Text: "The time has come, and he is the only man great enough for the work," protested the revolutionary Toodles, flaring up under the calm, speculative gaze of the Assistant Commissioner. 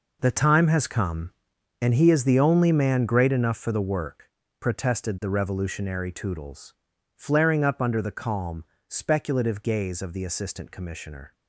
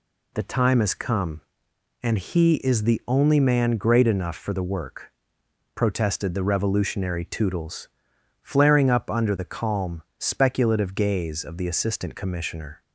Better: second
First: gets quieter; strong; throughout; 12.5 dB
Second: none

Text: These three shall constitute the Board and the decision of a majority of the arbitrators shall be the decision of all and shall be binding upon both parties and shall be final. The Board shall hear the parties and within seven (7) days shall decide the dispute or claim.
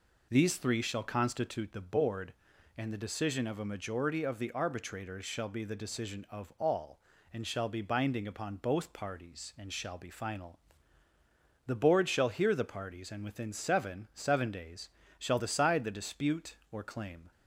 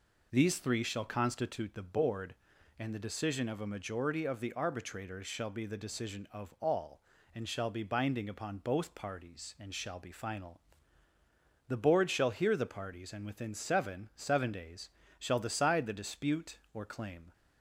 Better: neither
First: pauses between "days" and "shall"; slight; at 14.9 s; 0.28 s long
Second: pauses between "days" and "shall"; slight; at 14.9 s; 0.28 s long

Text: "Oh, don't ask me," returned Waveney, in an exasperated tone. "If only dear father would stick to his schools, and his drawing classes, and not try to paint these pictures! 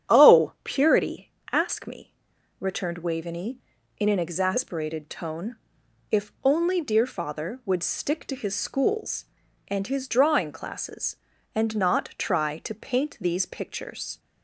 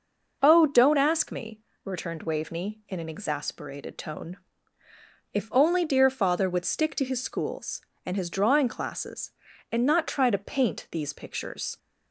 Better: second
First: starts louder than the rest; strong; until 1.2 s; 9 dB // says "purity" for "don't"; at 0.6 s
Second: none

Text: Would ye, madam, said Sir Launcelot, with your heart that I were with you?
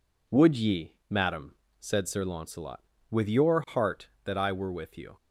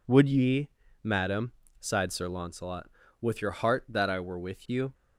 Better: first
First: none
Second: says "sighed" for "said"; at 1.7 s

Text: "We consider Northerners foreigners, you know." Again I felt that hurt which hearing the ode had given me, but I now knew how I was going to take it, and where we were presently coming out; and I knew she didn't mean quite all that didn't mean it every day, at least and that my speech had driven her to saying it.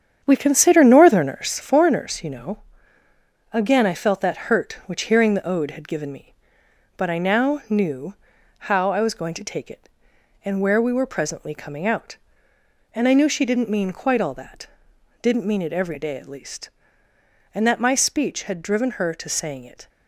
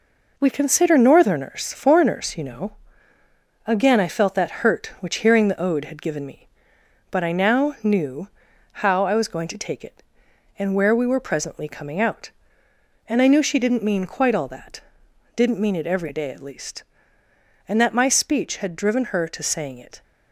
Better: second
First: starts louder than the rest; strong; until 1.7 s; 8.5 dB // pauses between "knew" and "how"; noticeable; at 8.1 s; 0.56 s long // pauses between "that" and "didn't"; noticeable; at 14.6 s; 0.54 s long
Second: pauses between "knew" and "how"; noticeable; at 8.2 s; 0.56 s long // pauses between "that" and "didn't"; noticeable; at 14.8 s; 0.54 s long

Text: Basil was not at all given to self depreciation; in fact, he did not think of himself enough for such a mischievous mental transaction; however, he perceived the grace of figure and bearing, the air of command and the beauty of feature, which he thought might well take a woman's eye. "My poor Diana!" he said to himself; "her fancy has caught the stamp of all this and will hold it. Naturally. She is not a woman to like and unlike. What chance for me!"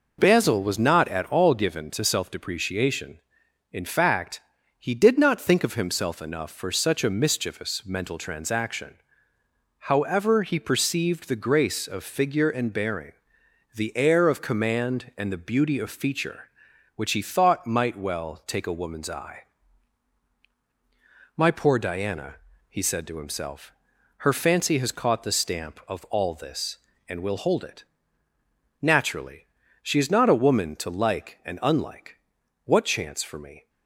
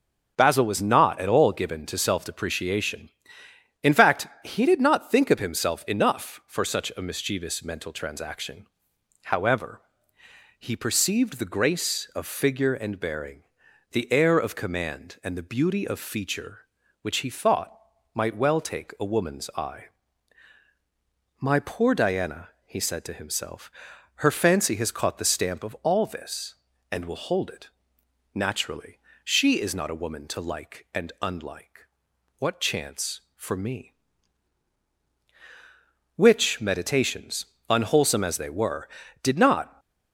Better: first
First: none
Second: starts louder than the rest; until 1.3 s; 7 dB // pauses between "thought" and "might"; at 17.7 s; 0.38 s long // goes on to say "Which meditations unwholesome as they were did not"; strong; from 36.1 s on; 3.6 s long

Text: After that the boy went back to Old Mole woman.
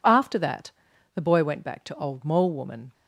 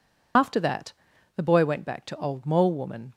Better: first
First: pauses between "that" and "the"; at 0.7 s; 0.42 s long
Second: loses the start of "After"; at 0.3 s; 110 ms // pauses between "that" and "the"; at 0.9 s; 0.42 s long

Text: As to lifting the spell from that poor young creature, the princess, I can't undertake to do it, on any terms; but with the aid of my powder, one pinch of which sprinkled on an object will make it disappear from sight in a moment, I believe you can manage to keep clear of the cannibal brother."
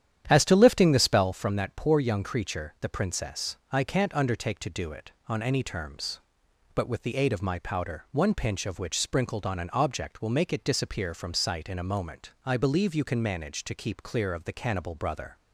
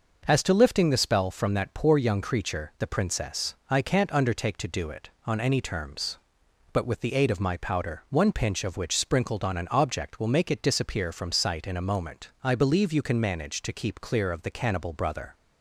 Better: second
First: starts louder than the rest; strong; until 1.5 s; 10 dB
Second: none

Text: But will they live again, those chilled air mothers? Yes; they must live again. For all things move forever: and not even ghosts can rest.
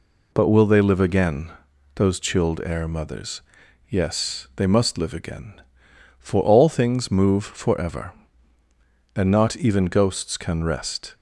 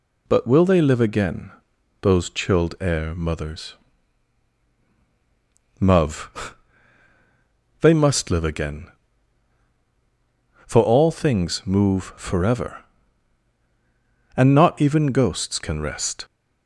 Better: first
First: none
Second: says "Muv" for "Yes"; at 5.7 s

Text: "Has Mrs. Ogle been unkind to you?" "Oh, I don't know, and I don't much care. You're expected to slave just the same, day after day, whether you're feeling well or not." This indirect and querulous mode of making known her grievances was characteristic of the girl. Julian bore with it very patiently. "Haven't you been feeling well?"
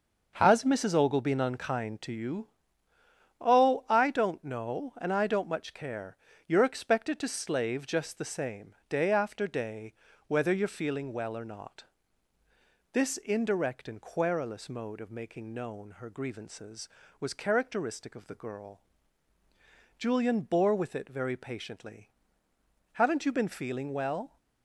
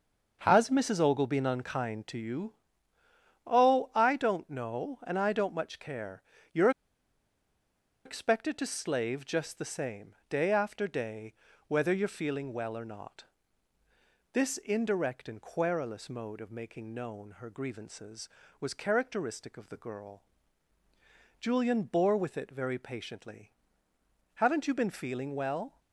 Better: first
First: starts louder than the rest; until 1.3 s; 6.5 dB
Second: starts louder than the rest; until 1.4 s; 6.5 dB // pauses between "You're" and "expected"; strong; at 6.6 s; 1.3 s long

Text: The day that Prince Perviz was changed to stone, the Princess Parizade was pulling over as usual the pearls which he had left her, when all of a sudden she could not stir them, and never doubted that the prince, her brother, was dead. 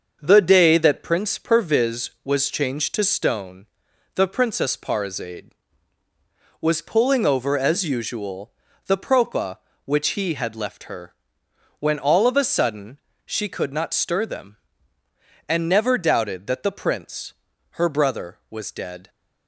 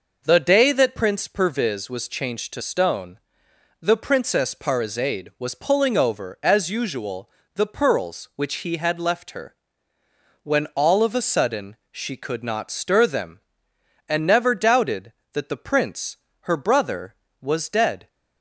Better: second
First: starts louder than the rest; until 1.2 s; 6.5 dB // pauses between "usual" and "the"; slight; at 8.5 s; 0.36 s long // says "propa" for "pearls"; at 8.9 s // pauses between "sudden" and "she"; slight; at 12.9 s; 0.28 s long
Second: pauses between "usual" and "the"; slight; at 7.2 s; 0.26 s long // pauses between "sudden" and "she"; slight; at 11.7 s; 0.16 s long

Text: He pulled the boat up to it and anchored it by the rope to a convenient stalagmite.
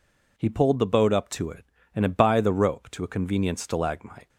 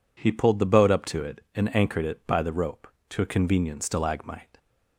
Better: second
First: skips "anchored"; at 2.0 s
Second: none

